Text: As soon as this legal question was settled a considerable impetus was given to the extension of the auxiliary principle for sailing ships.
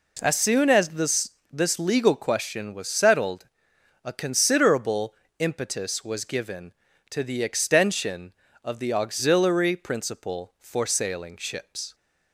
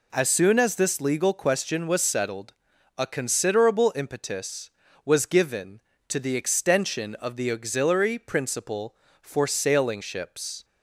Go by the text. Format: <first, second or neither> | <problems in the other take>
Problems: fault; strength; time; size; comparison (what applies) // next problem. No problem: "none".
second | says "this" twice; at 1.5 s // pauses between "settled" and "a"; noticeable; at 3.4 s; 0.58 s long; noticeable in the second // pauses between "considerable" and "impetus"; slight; at 5.1 s; 0.24 s long